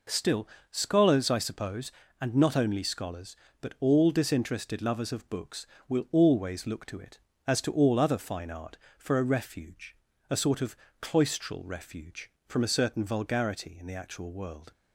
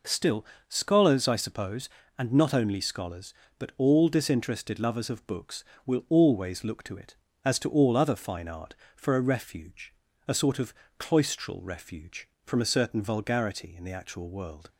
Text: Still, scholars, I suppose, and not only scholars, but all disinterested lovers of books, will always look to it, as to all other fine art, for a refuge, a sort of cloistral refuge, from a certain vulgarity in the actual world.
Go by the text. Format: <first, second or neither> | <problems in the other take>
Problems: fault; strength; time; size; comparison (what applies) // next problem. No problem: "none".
neither | pauses between "of" and "cloistral"; slight; the same in both